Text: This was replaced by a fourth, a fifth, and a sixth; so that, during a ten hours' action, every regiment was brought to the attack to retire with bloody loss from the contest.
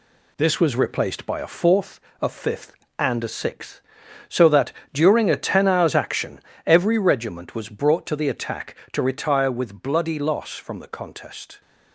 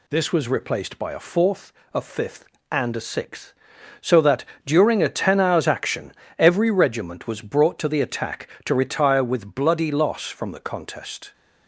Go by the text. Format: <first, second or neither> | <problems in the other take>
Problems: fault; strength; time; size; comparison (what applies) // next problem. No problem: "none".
second | gets quieter; noticeable; throughout; 5 dB